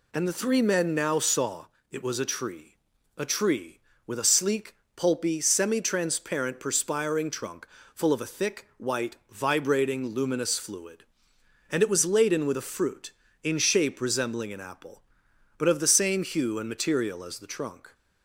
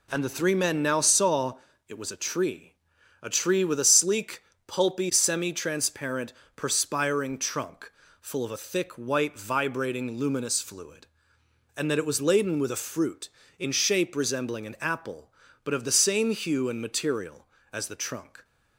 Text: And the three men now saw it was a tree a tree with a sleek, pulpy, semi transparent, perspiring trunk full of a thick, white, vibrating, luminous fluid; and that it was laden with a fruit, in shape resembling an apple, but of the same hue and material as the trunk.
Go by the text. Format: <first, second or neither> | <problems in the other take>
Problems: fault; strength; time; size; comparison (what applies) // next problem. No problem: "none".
second | pauses between "saw" and "it"; slight; at 1.6 s; 0.24 s long; slight in the second // pauses between "tree" and "a"; at 2.7 s; 0.40 s long; noticeable in the second // pauses between "trunk" and "full"; slight; at 7.6 s; 0.26 s long; slight in the second // skips "that"; at 11.8 s